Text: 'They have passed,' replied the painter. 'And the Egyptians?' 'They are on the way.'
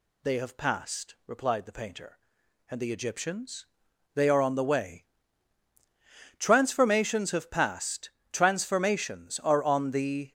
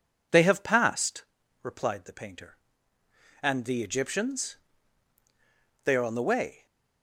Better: second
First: goes on to say "Transformations have passed transformations are on the"; strong; from 6.3 s on; 3.9 s long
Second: none

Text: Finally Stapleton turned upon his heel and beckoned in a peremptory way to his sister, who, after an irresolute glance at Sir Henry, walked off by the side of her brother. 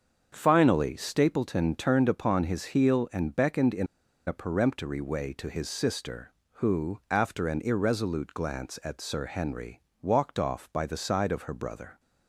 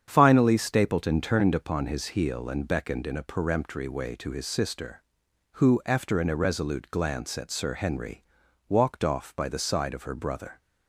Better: second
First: starts louder than the rest; until 1.3 s; 7 dB // pauses between "in" and "a"; at 3.8 s; 0.41 s long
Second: starts louder than the rest; strong; until 1.0 s; 8 dB

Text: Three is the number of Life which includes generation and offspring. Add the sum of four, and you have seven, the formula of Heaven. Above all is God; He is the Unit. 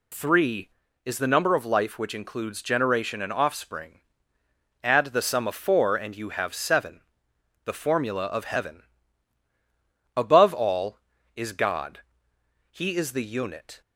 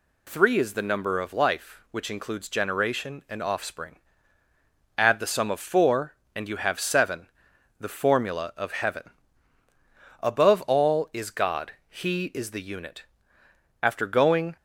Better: first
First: none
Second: goes on to say "After going"; noticeable; from 13.8 s on; 0.74 s long

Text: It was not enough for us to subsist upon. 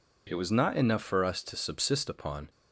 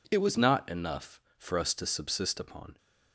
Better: neither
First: none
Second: none

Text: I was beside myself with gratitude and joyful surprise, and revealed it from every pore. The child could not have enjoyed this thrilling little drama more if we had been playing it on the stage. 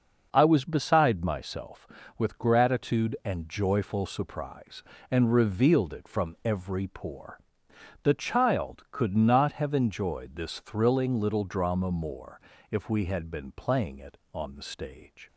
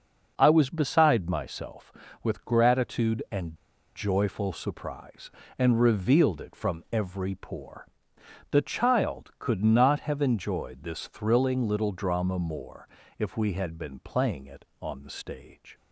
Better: first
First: starts louder than the rest; noticeable; until 1.3 s; 6 dB // pauses between "more" and "if"; slight; at 12.4 s; 0.30 s long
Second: starts louder than the rest; noticeable; until 1.3 s; 6 dB // pauses between "and" and "joyful"; at 3.5 s; 0.40 s long // pauses between "more" and "if"; slight; at 12.8 s; 0.30 s long

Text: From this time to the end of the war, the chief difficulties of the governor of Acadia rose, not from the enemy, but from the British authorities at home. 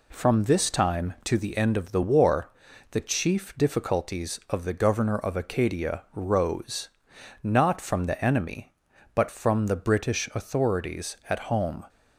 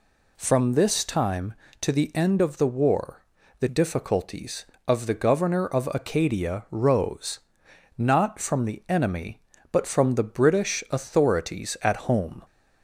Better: first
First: none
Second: skips "chief"; at 3.6 s

